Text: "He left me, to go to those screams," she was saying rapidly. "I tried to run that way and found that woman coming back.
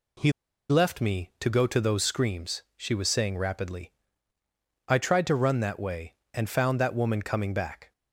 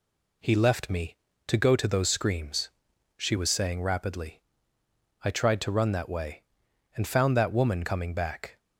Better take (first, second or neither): second